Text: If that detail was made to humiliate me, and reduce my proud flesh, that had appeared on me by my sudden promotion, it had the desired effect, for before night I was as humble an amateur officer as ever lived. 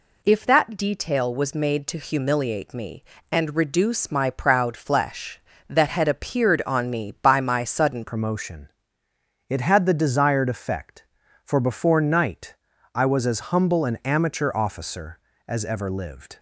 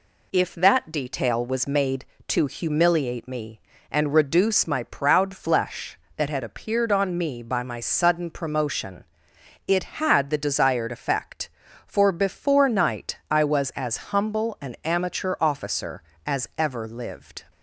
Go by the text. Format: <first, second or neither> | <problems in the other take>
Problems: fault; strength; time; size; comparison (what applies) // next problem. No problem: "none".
second | changes voice at "promotion"; from 8.0 s on; 8.3 s long // pauses between "night" and "I"; at 12.5 s; 0.38 s long